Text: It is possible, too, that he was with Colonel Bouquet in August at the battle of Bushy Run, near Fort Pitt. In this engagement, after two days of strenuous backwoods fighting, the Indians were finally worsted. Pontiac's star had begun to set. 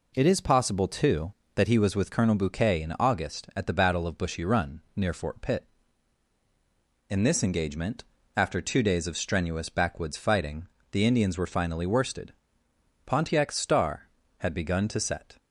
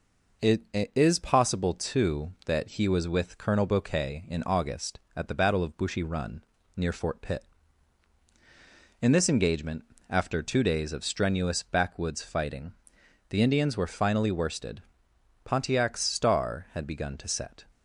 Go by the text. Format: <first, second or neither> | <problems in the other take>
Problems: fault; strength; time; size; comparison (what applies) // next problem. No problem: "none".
first | says "It" twice; at 0.7 s